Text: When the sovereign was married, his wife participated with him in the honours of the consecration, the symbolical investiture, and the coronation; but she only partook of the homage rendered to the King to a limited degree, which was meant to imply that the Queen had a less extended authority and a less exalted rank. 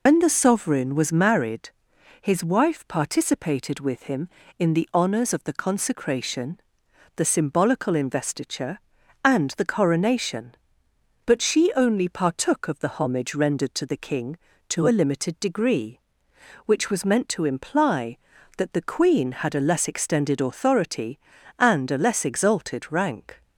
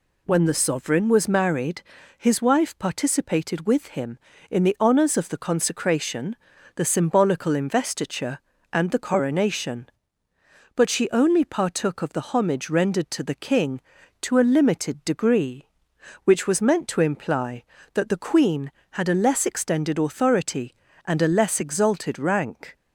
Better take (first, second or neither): second